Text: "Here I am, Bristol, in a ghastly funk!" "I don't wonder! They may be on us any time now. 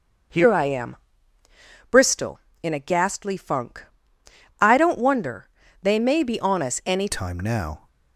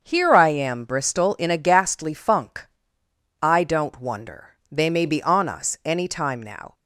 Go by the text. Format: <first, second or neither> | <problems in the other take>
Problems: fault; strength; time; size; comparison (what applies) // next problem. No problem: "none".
second | starts louder than the rest; until 2.2 s; 6.5 dB; also in the second // changes voice at "time"; from 7.1 s on; 0.7 s long